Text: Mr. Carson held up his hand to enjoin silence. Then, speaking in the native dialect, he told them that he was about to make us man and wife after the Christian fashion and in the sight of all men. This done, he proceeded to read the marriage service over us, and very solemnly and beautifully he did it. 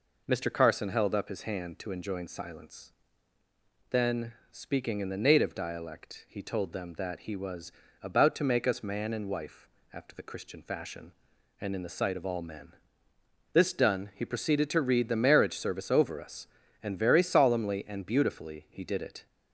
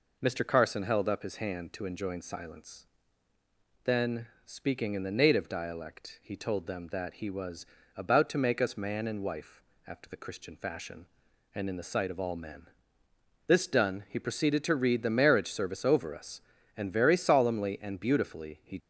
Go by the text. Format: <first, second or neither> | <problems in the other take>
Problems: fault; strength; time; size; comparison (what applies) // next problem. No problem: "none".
first | pauses between "was" and "about"; slight; at 7.6 s; 0.30 s long; slight in the first // pauses between "wife" and "after"; slight; at 9.6 s; 0.24 s long; slight in the first // stops before "did it"; at 18.7 s